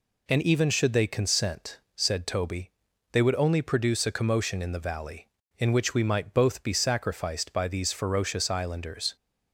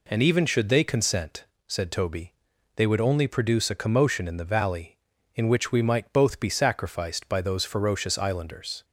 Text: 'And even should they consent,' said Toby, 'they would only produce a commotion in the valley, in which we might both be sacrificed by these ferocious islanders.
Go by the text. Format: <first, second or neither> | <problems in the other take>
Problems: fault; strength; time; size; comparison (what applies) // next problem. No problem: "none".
first | says "those" for "these"; at 7.4 s